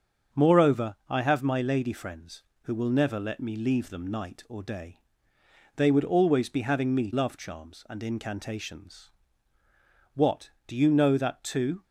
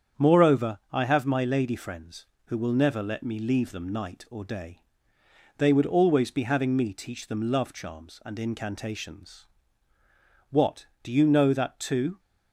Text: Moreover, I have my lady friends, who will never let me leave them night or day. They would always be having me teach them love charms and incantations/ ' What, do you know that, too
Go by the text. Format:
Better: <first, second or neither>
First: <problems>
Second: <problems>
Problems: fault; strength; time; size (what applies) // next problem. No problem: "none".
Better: second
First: starts louder than the rest; strong; until 1.4 s; 8 dB // skips "teach them"; at 7.1 s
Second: starts louder than the rest; strong; until 1.3 s; 8 dB